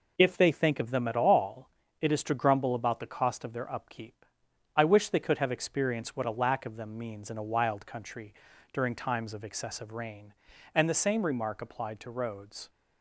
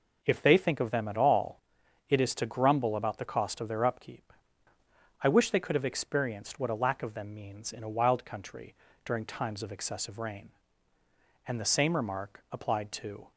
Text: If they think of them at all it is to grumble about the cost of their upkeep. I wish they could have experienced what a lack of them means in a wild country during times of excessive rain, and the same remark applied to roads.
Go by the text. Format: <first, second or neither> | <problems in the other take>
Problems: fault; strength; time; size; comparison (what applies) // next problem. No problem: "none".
first | pauses between "all" and "it"; noticeable; at 1.5 s; 0.48 s long; slight in the first // pauses between "country" and "during"; slight; at 8.7 s; 0.32 s long; also in the first // stops before "roads"; at 13.3 s